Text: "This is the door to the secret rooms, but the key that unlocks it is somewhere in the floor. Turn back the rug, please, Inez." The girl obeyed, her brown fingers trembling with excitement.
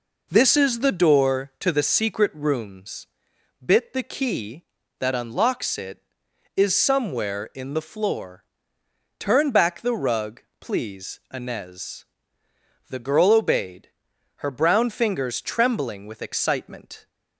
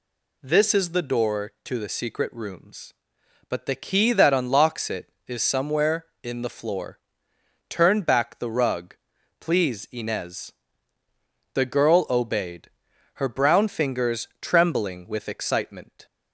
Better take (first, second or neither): second